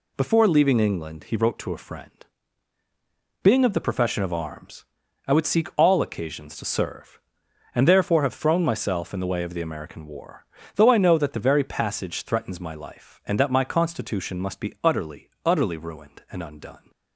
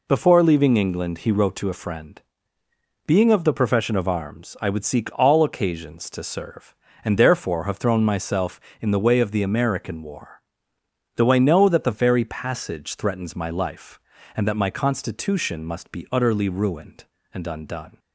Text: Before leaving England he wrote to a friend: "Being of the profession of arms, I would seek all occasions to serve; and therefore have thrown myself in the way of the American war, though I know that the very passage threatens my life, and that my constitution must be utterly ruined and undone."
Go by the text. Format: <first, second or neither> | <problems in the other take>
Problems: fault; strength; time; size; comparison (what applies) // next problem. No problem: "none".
second | says "utterly" twice; at 15.4 s